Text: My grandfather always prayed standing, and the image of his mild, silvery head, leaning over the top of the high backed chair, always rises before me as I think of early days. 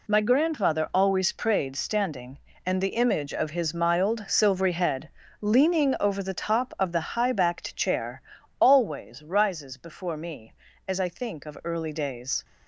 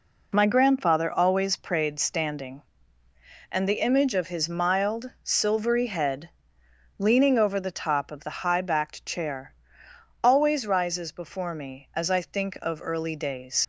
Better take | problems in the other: first | leaves "days" unfinished; at 13.6 s; 85 ms

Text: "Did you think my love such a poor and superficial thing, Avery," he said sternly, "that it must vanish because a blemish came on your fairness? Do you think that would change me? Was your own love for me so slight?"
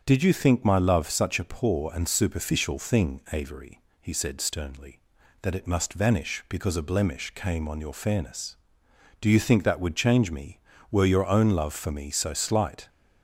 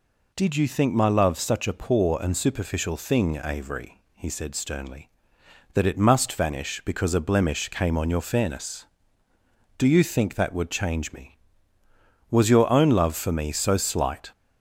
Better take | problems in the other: second | starts louder than the rest; strong; until 1.0 s; 7 dB // says "Were" for "Was"; at 10.9 s

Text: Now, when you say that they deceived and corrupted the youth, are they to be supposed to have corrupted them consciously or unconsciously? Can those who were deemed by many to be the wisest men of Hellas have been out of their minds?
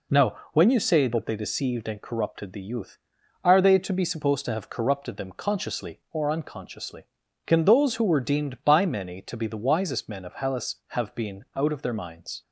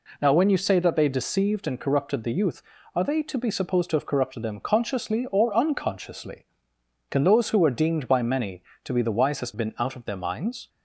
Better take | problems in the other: first | skips "men of Hellas have"; at 9.5 s

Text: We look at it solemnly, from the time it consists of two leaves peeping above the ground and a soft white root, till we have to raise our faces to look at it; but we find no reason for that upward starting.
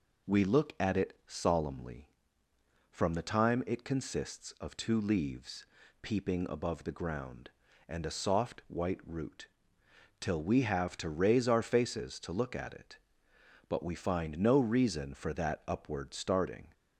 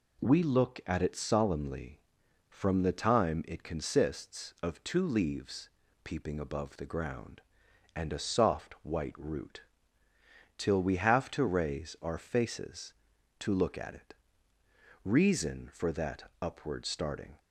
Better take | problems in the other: first | pauses between "leaves" and "peeping"; slight; at 5.6 s; 0.34 s long; slight in the first // skips "but we find no"; at 14.5 s

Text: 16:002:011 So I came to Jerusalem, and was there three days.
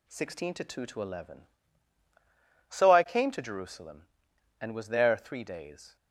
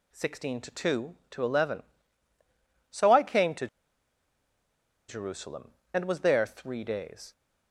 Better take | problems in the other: first | pauses between "to" and "Jerusalem"; strong; at 3.6 s; 1.4 s long

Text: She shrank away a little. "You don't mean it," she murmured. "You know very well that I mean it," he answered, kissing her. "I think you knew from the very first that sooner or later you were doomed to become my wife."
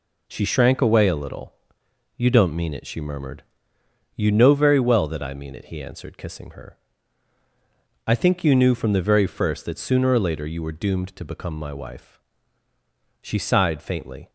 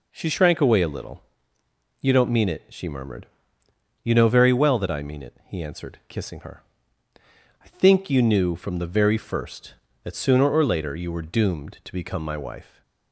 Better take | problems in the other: second | goes on to say "She sighed faintly"; noticeable; from 13.2 s on; 1.0 s long

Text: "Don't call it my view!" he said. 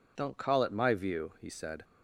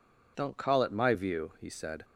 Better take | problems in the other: neither | none

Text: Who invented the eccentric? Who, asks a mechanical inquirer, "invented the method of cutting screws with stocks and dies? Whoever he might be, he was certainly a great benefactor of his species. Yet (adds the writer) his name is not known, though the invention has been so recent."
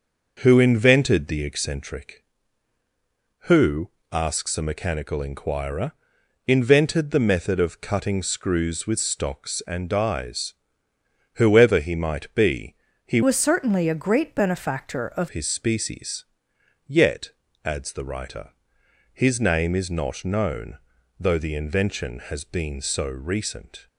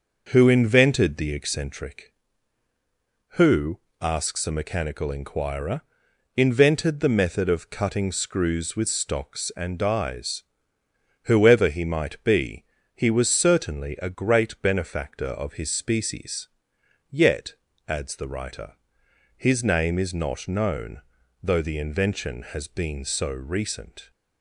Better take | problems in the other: second | starts louder than the rest; noticeable; until 1.4 s; 6 dB; noticeable in the second // changes voice from "was" to "of"; from 13.2 to 15.2 s; 2.0 s long

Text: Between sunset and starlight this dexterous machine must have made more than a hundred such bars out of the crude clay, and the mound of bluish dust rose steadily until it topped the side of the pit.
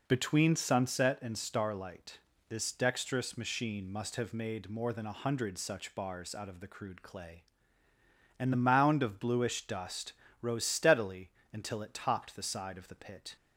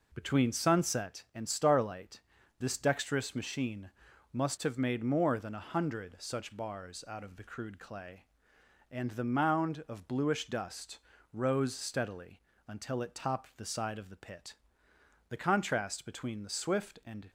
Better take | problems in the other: first | pauses between "starlight" and "this"; at 2.2 s; 0.38 s long; slight in the first // pauses between "machine" and "must"; at 3.9 s; 0.40 s long // pauses between "dust" and "rose"; slight; at 10.9 s; 0.34 s long; slight in the first // pauses between "steadily" and "until"; slight; at 12.3 s; 0.28 s long; slight in the first // goes on to say "The contrast between the swift and"; strong; from 15.2 s on; 2.0 s long

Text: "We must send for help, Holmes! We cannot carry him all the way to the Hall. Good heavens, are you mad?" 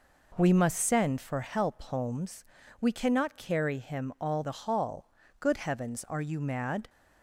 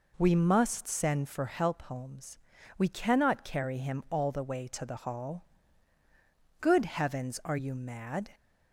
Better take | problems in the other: second | skips "the way to"; at 4.4 s

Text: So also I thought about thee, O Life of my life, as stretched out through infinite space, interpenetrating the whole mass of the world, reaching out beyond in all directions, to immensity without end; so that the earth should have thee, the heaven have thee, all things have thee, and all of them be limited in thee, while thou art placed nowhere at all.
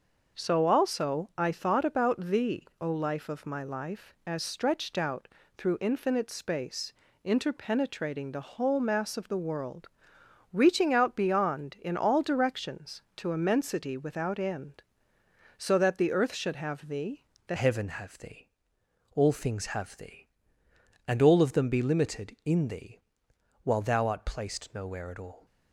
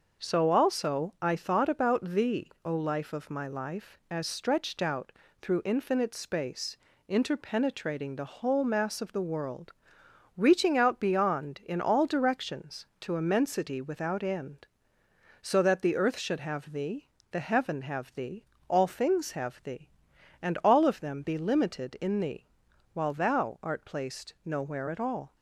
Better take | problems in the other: second | starts louder than the rest; until 1.4 s; 6 dB; also in the second // pauses between "out" and "through"; slight; at 5.2 s; 0.28 s long; slight in the second // changes voice at "heaven"; from 17.5 s on; 7.9 s long

